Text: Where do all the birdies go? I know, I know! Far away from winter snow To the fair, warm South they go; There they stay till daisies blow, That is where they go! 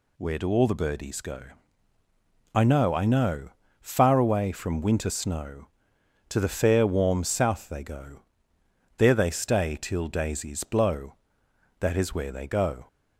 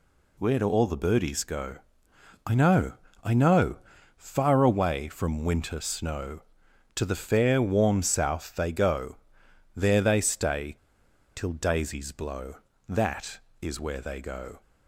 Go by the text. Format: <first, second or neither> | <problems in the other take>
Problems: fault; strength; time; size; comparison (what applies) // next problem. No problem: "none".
first | pauses between "stay" and "till"; noticeable; at 10.7 s; 0.58 s long